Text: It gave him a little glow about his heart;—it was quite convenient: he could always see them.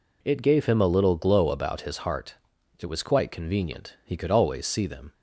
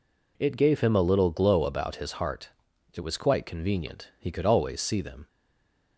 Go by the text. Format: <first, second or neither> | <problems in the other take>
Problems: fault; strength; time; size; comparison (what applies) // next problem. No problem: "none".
first | stays silent after the last word; slight; from 5.2 s on; 0.7 s long